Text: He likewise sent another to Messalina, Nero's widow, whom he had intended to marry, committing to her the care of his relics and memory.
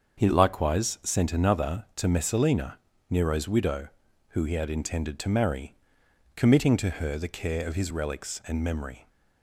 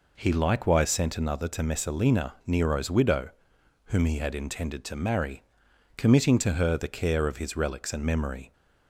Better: second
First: starts louder than the rest; until 1.2 s; 6.5 dB // says "who" for "whom"; at 4.3 s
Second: none

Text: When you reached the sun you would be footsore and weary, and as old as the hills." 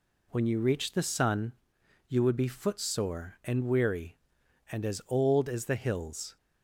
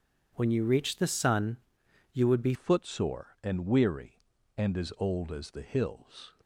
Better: first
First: pauses between "sun" and "you"; noticeable; at 1.5 s; 0.54 s long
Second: pauses between "sun" and "you"; noticeable; at 1.5 s; 0.54 s long // changes voice at "footsore"; from 2.5 s on; 3.8 s long

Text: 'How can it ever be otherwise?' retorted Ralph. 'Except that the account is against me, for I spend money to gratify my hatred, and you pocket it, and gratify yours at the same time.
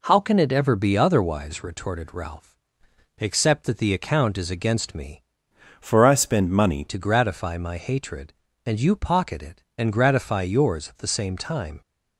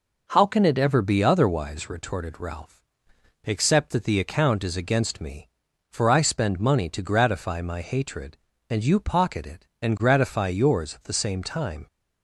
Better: second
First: changes voice from "for" to "money"; from 5.7 to 6.8 s; 1.1 s long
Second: none

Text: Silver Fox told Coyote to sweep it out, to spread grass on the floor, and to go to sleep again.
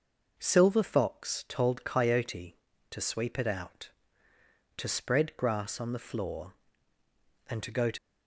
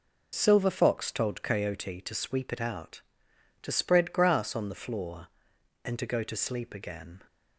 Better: second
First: stops before "sleep again"; at 7.9 s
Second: none

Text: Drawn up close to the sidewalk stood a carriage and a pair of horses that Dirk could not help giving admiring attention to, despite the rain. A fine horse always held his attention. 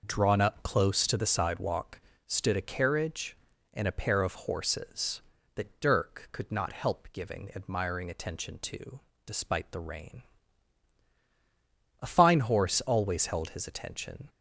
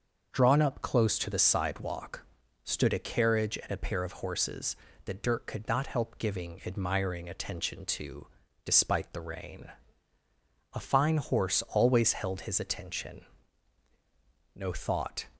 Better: first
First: pauses between "sidewalk" and "stood"; slight; at 2.0 s; 0.26 s long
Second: starts louder than the rest; noticeable; until 1.3 s; 6 dB // pauses between "sidewalk" and "stood"; at 2.2 s; 0.40 s long // goes on to say "No thought"; noticeable; from 14.5 s on; 0.70 s long

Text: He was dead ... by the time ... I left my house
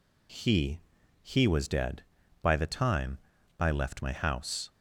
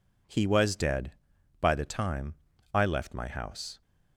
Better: second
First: says "He" twice; at 1.2 s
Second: none

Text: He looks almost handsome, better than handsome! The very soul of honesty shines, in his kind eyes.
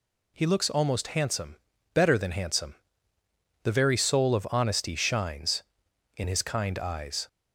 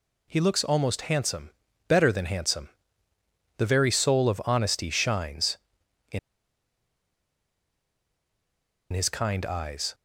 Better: first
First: none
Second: pauses between "in" and "his"; strong; at 6.1 s; 2.7 s long

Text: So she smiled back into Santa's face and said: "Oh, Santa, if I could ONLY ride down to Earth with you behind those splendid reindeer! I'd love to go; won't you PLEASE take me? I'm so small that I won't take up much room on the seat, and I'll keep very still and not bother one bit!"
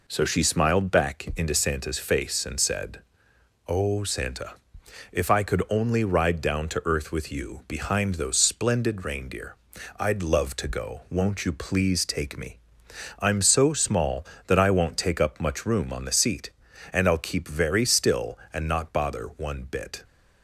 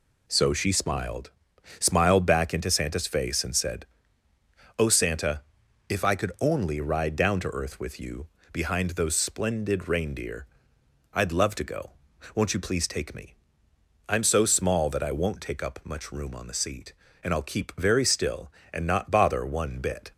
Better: first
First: none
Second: says "smiled" twice; at 1.7 s // pauses between "you" and "behind"; slight; at 8.2 s; 0.26 s long

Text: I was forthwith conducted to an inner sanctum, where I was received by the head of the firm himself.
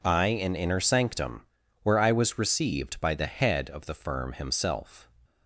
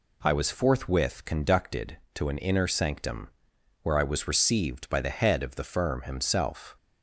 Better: second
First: skips "was forthwith conducted to"; at 0.2 s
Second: none

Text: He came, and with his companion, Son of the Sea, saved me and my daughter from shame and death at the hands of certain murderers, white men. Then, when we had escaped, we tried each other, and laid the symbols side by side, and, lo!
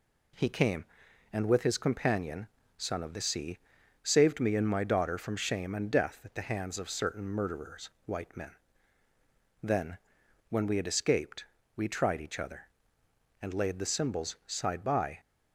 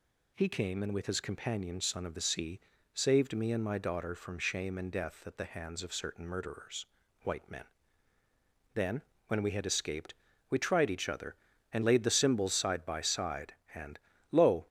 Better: second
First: stops before "side and lo"; at 15.1 s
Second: none

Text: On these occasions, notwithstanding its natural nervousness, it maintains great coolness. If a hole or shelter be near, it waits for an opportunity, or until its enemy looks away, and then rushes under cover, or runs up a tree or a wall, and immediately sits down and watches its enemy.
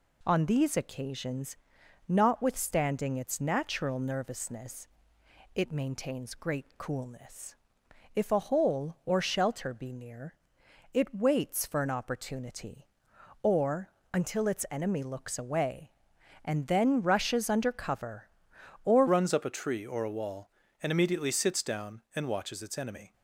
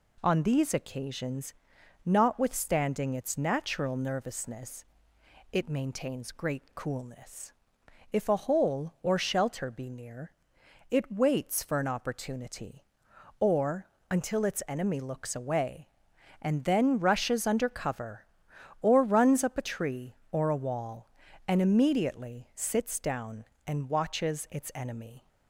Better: second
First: pauses between "or" and "until"; slight; at 13.8 s; 0.24 s long // changes voice at "runs"; from 19.0 s on; 4.1 s long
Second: pauses between "or" and "until"; slight; at 13.8 s; 0.24 s long

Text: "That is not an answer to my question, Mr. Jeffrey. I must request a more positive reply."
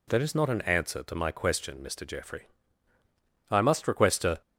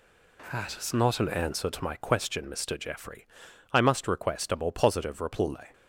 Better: second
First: stops before "more positive reply"; at 4.4 s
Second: none

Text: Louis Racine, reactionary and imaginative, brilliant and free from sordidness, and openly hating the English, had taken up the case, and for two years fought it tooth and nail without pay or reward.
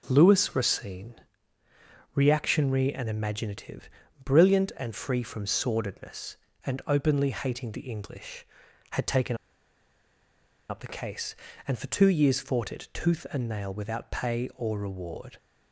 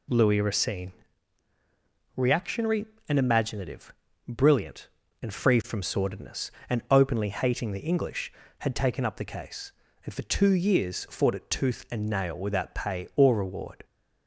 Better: second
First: starts louder than the rest; until 1.1 s; 6.5 dB // pauses between "taken" and "up"; strong; at 9.3 s; 1.3 s long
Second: none

